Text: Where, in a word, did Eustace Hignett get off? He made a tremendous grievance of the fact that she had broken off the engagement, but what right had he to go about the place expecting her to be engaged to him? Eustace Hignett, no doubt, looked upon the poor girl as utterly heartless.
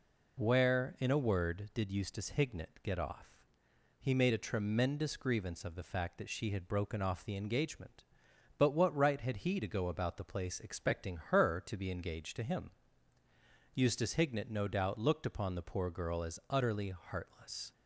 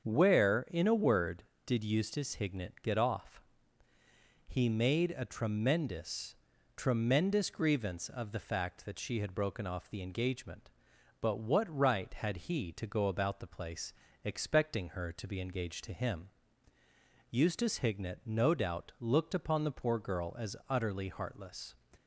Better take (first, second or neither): first